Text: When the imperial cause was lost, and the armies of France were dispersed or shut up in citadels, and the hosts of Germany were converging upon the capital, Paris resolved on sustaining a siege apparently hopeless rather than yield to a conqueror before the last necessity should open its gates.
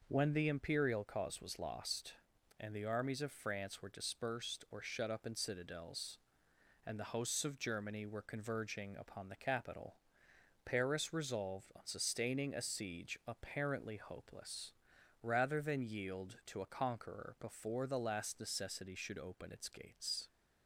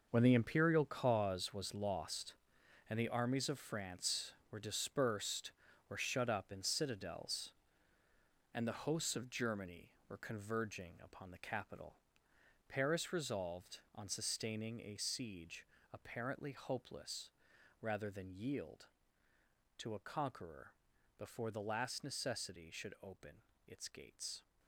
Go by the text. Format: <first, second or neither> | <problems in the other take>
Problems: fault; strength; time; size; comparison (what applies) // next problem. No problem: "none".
first | gets quieter; strong; throughout; 12 dB // pauses between "siege" and "apparently"; slight; at 15.6 s; 0.26 s long // pauses between "hopeless" and "rather"; noticeable; at 17.2 s; 0.52 s long; noticeable in the first // pauses between "conqueror" and "before"; noticeable; at 20.7 s; 0.46 s long // pauses between "open" and "its"; slight; at 23.4 s; 0.24 s long